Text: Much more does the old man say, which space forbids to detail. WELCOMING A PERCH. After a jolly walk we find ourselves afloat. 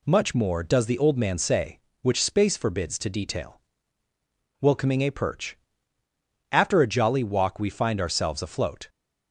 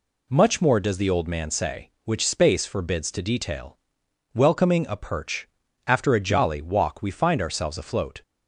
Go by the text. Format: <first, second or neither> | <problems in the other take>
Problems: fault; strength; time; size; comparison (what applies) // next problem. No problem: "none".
neither | none